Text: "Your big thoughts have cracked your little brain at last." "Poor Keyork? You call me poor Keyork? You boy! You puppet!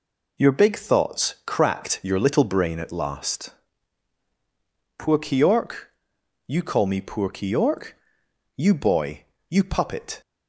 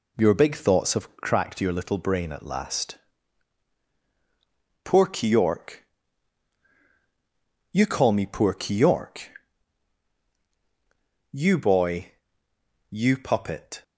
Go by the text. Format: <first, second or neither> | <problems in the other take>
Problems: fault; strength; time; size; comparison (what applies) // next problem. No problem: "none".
second | skips "have"; at 1.4 s